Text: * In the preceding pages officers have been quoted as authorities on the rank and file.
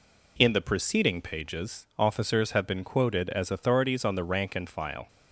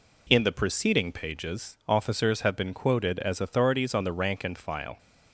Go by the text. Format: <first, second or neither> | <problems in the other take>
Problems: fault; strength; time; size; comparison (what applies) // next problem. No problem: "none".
neither | none